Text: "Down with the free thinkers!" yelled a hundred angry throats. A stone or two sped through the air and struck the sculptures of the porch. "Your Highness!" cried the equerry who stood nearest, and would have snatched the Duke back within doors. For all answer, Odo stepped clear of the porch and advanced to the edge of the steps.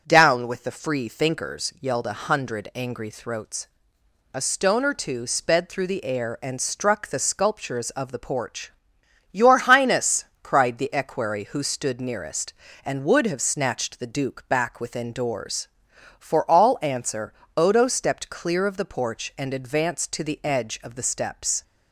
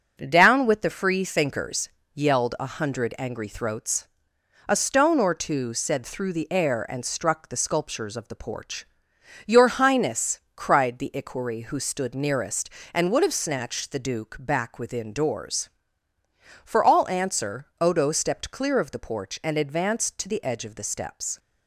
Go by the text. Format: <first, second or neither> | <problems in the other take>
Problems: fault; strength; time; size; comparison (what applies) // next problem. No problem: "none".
first | starts louder than the rest; until 1.2 s; 6 dB; strong in the first // says "said" for "sped"; at 5.7 s